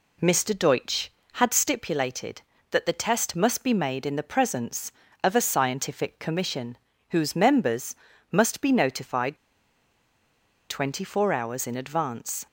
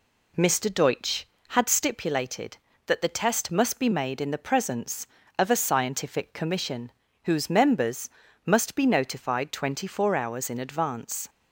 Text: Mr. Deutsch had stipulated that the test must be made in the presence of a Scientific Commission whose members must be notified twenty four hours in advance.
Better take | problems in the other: second | pauses between "Commission" and "whose"; slight; at 6.7 s; 0.34 s long; slight in the second // pauses between "members" and "must"; slight; at 7.9 s; 0.36 s long; slight in the second // pauses between "notified" and "twenty"; strong; at 9.3 s; 1.3 s long

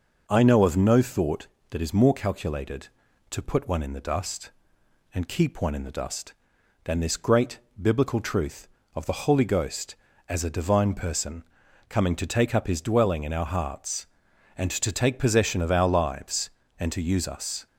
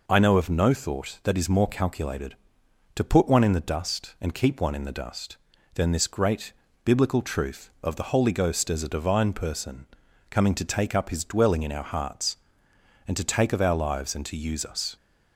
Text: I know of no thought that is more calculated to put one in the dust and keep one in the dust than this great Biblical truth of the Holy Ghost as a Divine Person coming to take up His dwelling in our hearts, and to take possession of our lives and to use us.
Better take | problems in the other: first | pauses between "great" and "Biblical"; slight; at 6.5 s; 0.32 s long; slight in the first // pauses between "Person" and "coming"; at 9.8 s; 0.44 s long; also in the first // skips "possession"; at 13.5 s

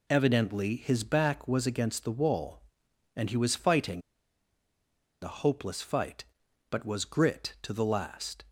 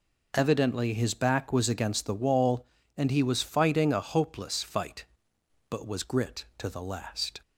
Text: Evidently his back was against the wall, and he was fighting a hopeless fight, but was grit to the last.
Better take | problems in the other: second | pauses between "fighting" and "a"; at 4.0 s; 1.2 s long

